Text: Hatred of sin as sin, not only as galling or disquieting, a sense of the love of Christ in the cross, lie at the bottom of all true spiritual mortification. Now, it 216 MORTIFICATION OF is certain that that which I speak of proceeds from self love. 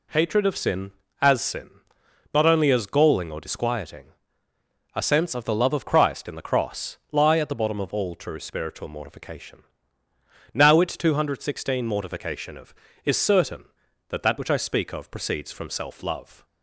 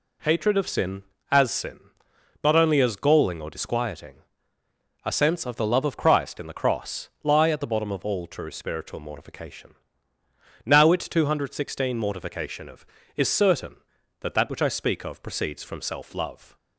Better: neither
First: none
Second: none

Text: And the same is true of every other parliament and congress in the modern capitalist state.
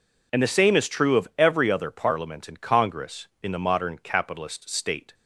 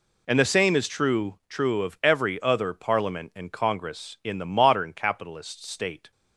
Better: first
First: none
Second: says "true" twice; at 1.4 s

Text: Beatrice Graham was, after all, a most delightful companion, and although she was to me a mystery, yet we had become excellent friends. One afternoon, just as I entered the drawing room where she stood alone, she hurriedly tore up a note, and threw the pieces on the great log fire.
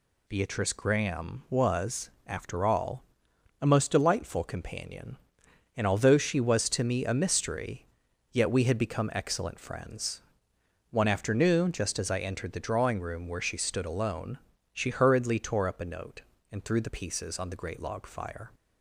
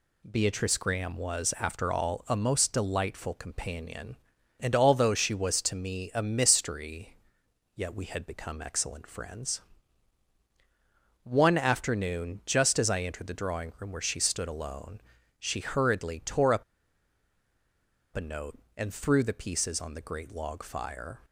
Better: first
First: none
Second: pauses between "up" and "a"; strong; at 16.6 s; 1.5 s long

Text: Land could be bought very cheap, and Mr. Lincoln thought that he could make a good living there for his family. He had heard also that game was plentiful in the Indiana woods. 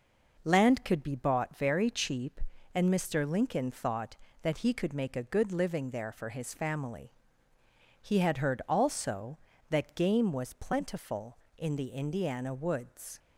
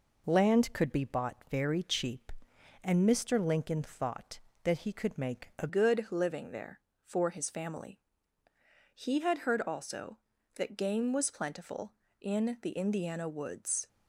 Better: first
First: none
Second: changes voice at "good"; from 5.6 s on; 8.2 s long

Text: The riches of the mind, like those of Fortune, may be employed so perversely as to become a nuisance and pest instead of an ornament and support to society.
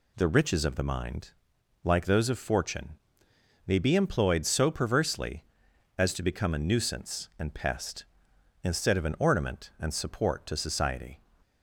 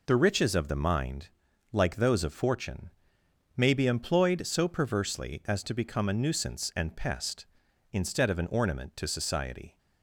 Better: first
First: none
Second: skips "and support"; at 8.9 s

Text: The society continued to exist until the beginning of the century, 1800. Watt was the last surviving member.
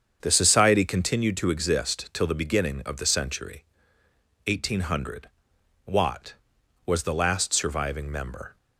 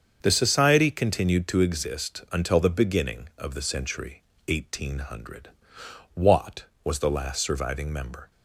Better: second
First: starts louder than the rest; strong; until 1.2 s; 7.5 dB // says "till" for "until"; at 2.1 s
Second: starts louder than the rest; until 1.2 s; 7 dB

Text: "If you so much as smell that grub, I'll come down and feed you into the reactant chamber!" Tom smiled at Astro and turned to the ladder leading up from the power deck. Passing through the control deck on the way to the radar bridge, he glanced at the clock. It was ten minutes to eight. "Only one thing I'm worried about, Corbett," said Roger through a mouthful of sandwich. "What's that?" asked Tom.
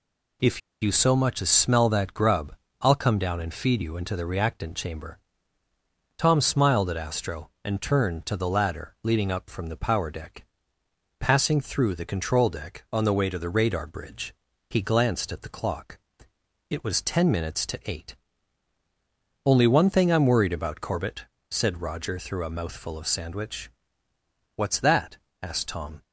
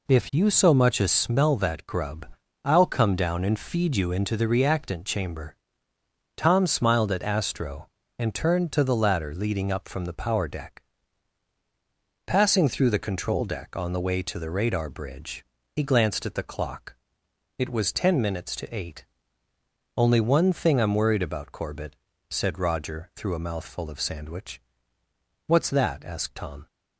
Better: second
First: pauses between "If" and "you"; slight; at 0.5 s; 0.22 s long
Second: none

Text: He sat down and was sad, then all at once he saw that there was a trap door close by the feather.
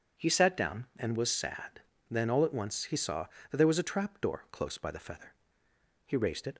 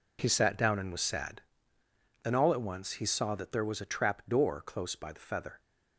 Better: second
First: starts louder than the rest; strong; until 1.2 s; 7 dB // goes on to say "He raised it"; from 6.0 s on; 0.50 s long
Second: none

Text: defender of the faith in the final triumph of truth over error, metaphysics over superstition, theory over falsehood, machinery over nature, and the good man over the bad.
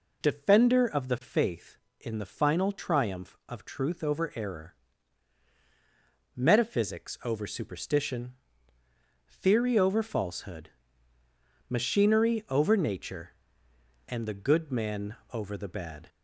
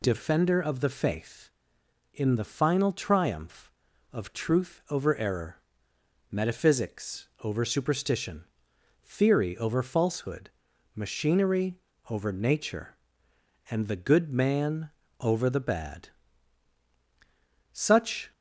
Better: first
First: pauses between "man" and "over"; slight; at 15.1 s; 0.16 s long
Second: pauses between "machinery" and "over"; slight; at 11.7 s; 0.34 s long // pauses between "man" and "over"; slight; at 14.8 s; 0.32 s long // goes on to say "Such"; from 17.7 s on; 0.60 s long

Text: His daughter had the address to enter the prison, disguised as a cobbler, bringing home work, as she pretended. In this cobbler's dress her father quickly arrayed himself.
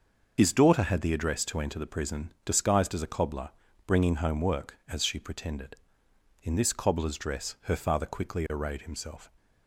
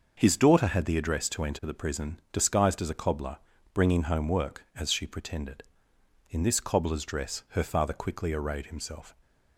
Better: second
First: loses the start of "His"; at 0.3 s; 50 ms // starts louder than the rest; until 1.3 s; 6 dB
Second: starts louder than the rest; until 1.1 s; 6 dB

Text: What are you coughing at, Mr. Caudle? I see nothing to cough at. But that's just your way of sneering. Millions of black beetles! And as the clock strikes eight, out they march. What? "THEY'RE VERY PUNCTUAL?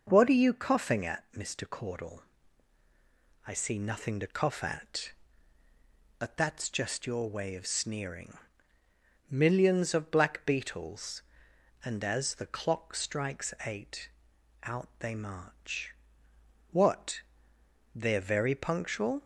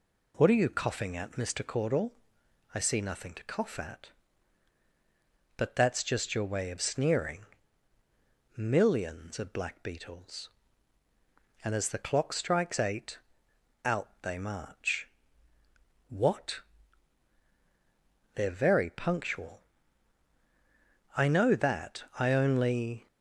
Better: first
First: none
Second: goes on to say "I know that I only"; strong; from 21.1 s on; 1.9 s long

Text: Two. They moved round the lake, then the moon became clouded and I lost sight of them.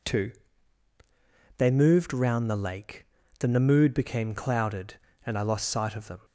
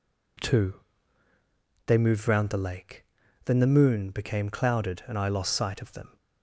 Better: second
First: says "mood" for "moon"; at 3.5 s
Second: none

